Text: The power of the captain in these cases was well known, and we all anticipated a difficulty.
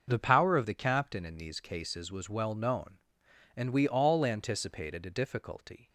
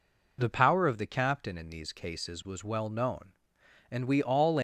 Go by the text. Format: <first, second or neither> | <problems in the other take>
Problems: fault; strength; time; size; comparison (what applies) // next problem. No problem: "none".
first | stops before "anticipated a difficulty"; at 4.5 s